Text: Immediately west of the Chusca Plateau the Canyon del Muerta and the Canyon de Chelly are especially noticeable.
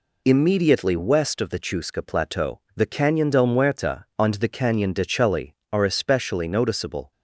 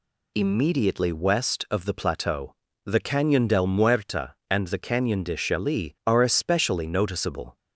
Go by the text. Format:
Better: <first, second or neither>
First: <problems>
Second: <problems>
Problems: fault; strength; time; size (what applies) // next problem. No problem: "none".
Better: first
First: pauses between "Plateau" and "the"; slight; at 2.5 s; 0.16 s long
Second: skips "Chusca"; at 1.9 s // pauses between "Plateau" and "the"; slight; at 2.5 s; 0.32 s long